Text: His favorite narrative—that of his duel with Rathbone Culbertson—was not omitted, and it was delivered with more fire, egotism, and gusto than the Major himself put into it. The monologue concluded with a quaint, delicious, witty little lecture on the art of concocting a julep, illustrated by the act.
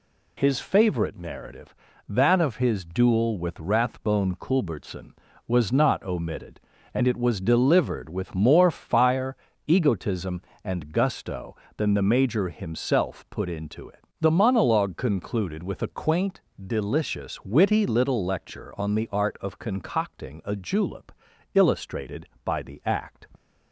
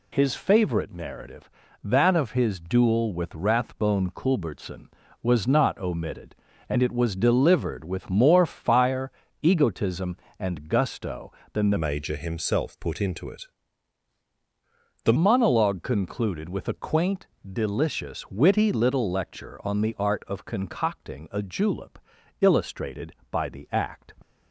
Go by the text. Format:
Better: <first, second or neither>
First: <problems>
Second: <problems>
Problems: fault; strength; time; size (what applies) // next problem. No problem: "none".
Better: first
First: none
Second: changes voice from "Major" to "The"; from 11.7 to 15.1 s; 3.4 s long